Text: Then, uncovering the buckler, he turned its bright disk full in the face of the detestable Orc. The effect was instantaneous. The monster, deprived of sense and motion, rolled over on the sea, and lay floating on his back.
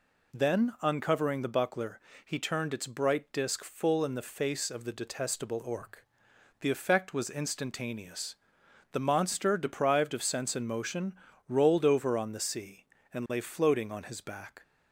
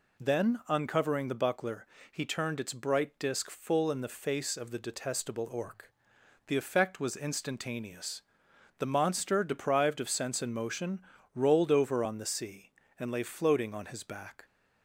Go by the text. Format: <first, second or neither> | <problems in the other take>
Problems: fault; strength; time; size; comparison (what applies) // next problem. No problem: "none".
neither | none